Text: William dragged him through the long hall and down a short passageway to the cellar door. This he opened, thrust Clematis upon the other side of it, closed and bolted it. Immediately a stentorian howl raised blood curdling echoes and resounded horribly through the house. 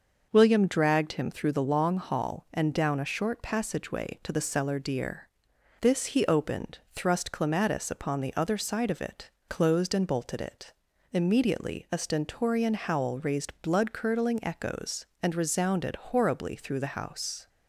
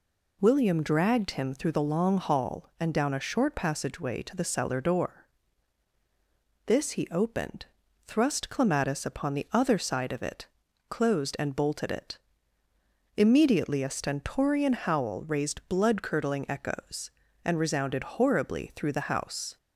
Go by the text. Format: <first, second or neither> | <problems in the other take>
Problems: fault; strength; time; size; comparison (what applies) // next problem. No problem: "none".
second | says "deer" for "door"; at 4.7 s